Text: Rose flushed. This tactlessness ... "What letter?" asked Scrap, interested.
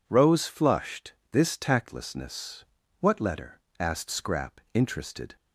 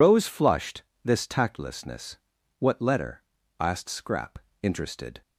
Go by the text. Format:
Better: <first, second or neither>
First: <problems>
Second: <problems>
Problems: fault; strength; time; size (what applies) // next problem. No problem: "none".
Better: first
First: none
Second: loses the start of "Rose"; at 0.0 s; 90 ms